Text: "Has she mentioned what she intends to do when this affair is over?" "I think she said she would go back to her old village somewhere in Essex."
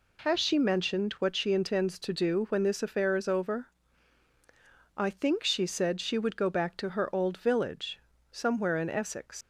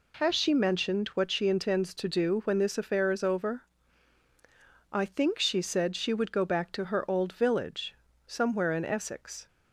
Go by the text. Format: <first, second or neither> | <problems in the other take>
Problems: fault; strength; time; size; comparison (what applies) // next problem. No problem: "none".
second | pauses between "village" and "somewhere"; slight; at 7.9 s; 0.30 s long; slight in the second // leaves "Essex" unfinished; at 9.4 s; 110 ms